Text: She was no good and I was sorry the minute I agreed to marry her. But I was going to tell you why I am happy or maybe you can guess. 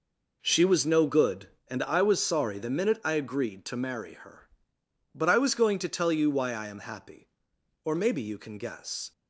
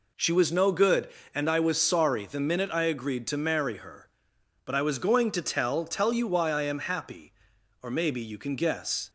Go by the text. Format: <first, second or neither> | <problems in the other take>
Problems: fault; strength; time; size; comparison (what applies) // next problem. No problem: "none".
first | says "tell" twice; at 5.8 s